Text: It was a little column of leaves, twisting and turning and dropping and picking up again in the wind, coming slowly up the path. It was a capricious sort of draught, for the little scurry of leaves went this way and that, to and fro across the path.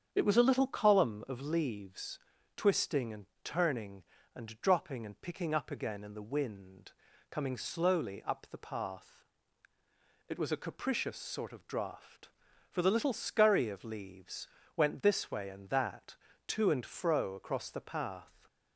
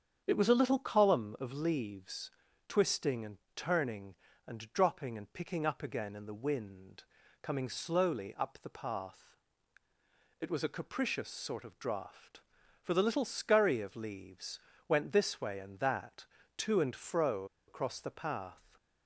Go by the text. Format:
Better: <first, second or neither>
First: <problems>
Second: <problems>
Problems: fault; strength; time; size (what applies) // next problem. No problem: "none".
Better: first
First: starts louder than the rest; strong; until 1.1 s; 8 dB // pauses between "and" and "turning"; slight; at 3.2 s; 0.20 s long // pauses between "leaves" and "went"; slight; at 14.4 s; 0.28 s long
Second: starts louder than the rest; strong; until 1.2 s; 8 dB // pauses between "and" and "turning"; slight; at 3.3 s; 0.20 s long // pauses between "leaves" and "went"; slight; at 14.5 s; 0.28 s long // pauses between "fro" and "across"; slight; at 17.4 s; 0.22 s long